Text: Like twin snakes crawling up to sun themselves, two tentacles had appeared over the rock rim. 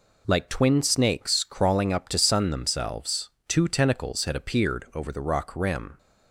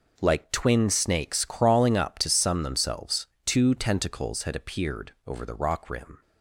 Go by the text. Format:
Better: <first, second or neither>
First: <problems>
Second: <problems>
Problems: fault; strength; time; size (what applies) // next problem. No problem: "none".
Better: neither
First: none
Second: none